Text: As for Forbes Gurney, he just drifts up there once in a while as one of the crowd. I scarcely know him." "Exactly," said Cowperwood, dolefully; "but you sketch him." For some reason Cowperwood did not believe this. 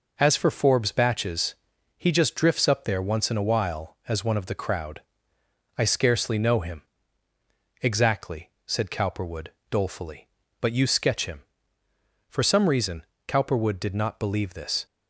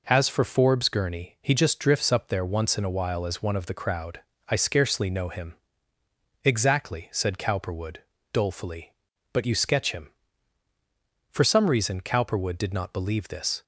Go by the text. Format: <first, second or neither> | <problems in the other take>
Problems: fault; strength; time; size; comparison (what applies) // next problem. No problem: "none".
second | says "Batches" for "Gurney"; at 0.9 s // pauses between "reason" and "Cowperwood"; slight; at 13.0 s; 0.24 s long